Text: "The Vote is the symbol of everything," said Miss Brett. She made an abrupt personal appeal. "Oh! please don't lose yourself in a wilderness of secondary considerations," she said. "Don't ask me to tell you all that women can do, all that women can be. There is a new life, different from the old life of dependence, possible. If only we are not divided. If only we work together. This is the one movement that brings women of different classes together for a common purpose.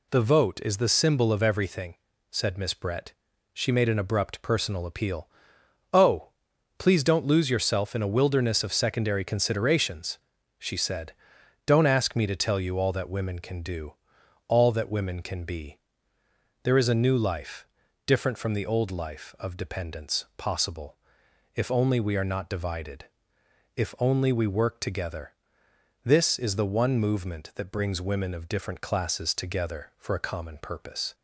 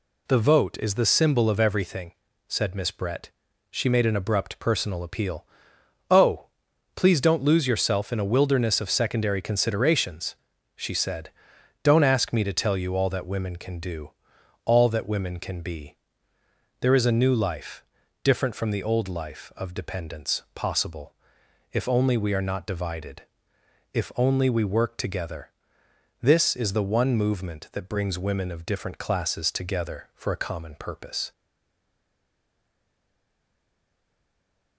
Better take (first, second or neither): first